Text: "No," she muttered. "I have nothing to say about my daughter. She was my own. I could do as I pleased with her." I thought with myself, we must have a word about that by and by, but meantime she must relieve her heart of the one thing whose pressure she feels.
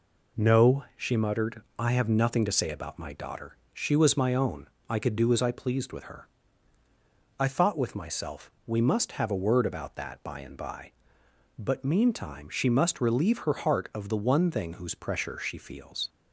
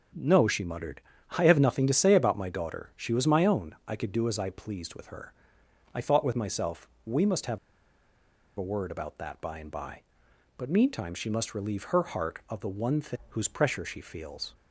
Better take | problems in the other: first | starts louder than the rest; strong; until 1.5 s; 7.5 dB // pauses between "have" and "a"; at 7.5 s; 0.99 s long

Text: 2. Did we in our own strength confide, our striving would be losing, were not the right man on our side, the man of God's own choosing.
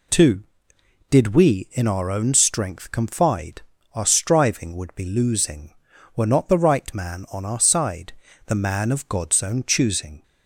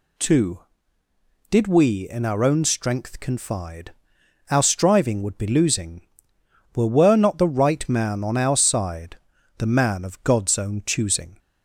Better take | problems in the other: first | says "were" twice; at 6.8 s

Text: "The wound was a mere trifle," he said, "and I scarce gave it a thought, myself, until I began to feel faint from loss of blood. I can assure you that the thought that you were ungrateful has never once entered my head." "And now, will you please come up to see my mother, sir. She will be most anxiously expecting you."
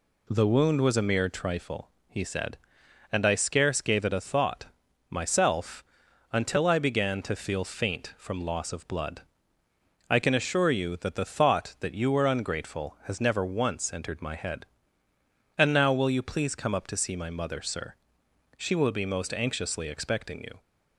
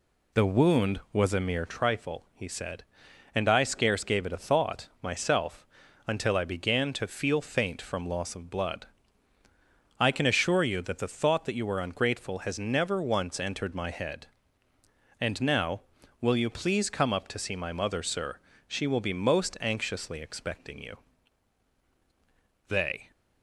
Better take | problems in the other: first | goes on to say "They"; slight; from 22.6 s on; 0.42 s long

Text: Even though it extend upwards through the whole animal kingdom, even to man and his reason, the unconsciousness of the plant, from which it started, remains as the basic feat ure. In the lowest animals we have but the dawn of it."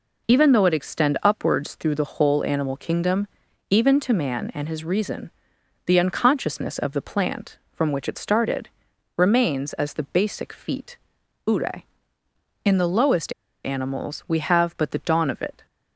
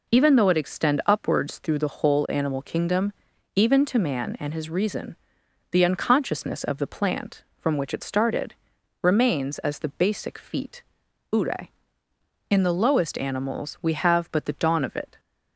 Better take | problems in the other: second | pauses between "feat" and "ure"; noticeable; at 10.9 s; 0.50 s long; noticeable in the second // pauses between "lowest" and "animals"; slight; at 13.3 s; 0.32 s long

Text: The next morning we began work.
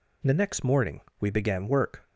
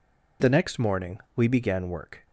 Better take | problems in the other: neither | pauses between "morning" and "we"; slight; the same in both

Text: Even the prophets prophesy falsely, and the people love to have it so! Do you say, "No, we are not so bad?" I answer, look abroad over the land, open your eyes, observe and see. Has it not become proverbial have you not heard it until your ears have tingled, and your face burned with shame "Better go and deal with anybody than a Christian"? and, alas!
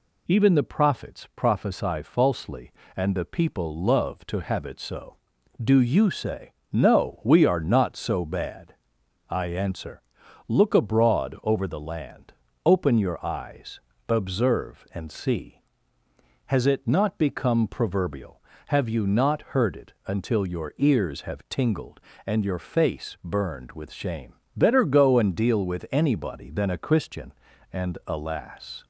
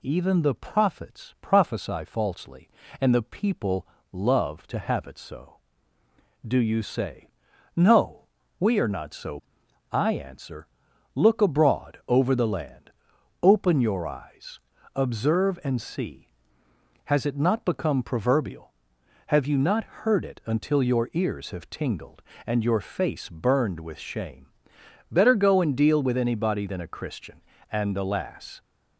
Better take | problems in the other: first | pauses between "people" and "love"; slight; at 3.8 s; 0.24 s long // skips "bad"; at 9.6 s // pauses between "shame" and "Better"; noticeable; at 24.4 s; 0.66 s long; slight in the first

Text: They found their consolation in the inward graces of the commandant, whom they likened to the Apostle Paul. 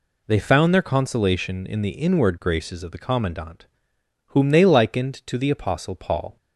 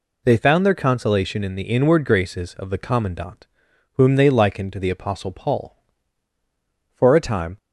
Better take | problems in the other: first | goes on to say "For a time"; noticeable; from 6.9 s on; 0.64 s long

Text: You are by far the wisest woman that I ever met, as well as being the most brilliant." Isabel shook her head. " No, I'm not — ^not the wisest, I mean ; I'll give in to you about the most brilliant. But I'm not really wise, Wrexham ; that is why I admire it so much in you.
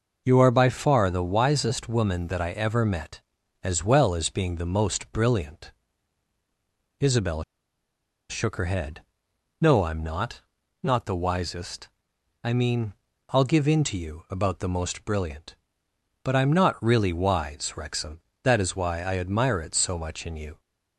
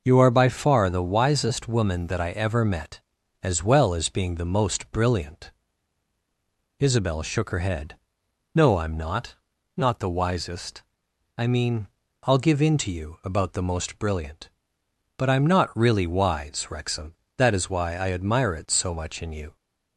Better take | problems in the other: second | pauses between "Isabel" and "shook"; noticeable; at 7.4 s; 0.86 s long

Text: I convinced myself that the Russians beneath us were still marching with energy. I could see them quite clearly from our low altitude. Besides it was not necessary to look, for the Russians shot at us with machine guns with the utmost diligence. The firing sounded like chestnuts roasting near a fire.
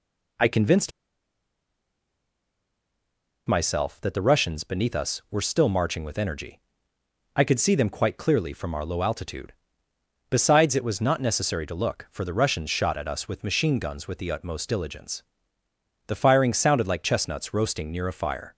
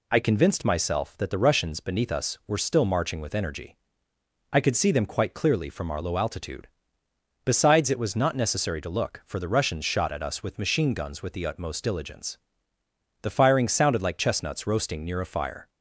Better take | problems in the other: second | pauses between "convinced" and "myself"; strong; at 0.9 s; 2.5 s long

